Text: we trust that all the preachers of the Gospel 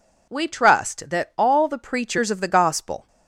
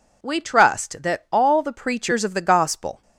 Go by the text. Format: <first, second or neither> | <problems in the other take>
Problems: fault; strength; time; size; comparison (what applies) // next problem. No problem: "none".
neither | none